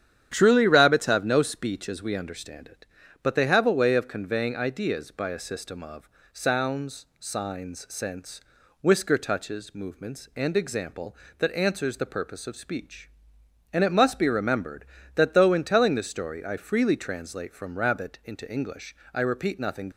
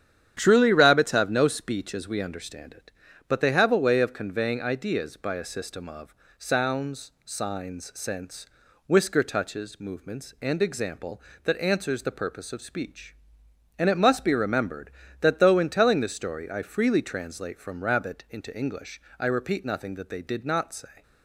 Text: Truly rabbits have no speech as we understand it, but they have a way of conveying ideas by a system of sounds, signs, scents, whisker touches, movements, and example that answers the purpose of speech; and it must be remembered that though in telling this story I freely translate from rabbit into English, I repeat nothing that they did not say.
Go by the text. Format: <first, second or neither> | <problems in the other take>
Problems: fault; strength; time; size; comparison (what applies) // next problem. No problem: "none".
second | starts louder than the rest; strong; until 1.3 s; 9.5 dB; strong in the second // pauses between "of" and "sounds"; slight; at 6.0 s; 0.24 s long; slight in the second // stops before "that they did not say"; at 19.9 s